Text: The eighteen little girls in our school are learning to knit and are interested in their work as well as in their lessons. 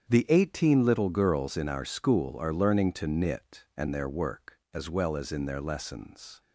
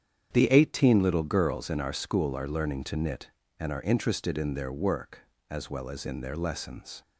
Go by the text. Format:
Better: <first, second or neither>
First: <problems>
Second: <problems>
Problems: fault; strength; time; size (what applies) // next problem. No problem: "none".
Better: second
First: starts louder than the rest; strong; until 1.1 s; 8 dB // skips "are interested in"; at 3.8 s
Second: starts louder than the rest; strong; until 1.3 s; 8.5 dB